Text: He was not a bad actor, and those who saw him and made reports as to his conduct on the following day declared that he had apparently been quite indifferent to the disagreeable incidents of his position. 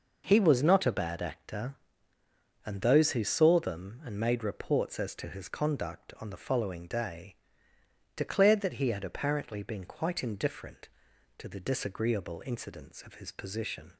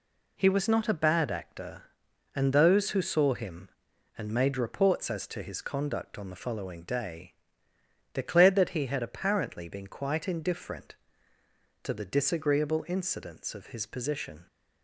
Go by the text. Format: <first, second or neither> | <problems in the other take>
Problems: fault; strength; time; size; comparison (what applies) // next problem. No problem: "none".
second | says "them" for "him"; at 3.5 s // pauses between "day" and "declared"; noticeable; at 7.3 s; 0.80 s long; noticeable in the second